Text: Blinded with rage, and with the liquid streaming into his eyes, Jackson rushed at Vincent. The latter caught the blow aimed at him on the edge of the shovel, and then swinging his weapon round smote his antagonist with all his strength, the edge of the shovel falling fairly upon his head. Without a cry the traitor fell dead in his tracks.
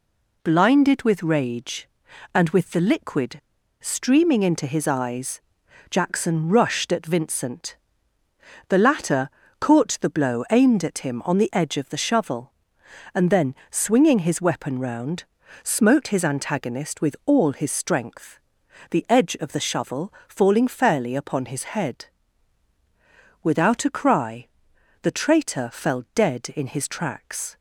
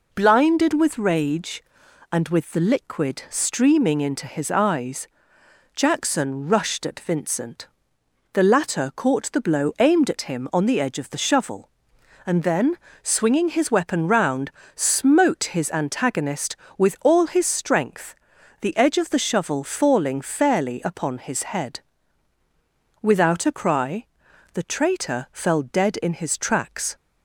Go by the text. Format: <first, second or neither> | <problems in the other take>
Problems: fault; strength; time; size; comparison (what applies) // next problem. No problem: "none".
second | pauses between "liquid" and "streaming"; at 3.3 s; 0.44 s long // pauses between "latter" and "caught"; slight; at 9.2 s; 0.30 s long // pauses between "then" and "swinging"; slight; at 13.5 s; 0.16 s long; slight in the second // pauses between "round" and "smote"; at 15.2 s; 0.38 s long; slight in the second // pauses between "shovel" and "falling"; slight; at 20.1 s; 0.18 s long // pauses between "cry" and "the"; noticeable; at 24.4 s; 0.56 s long; noticeable in the second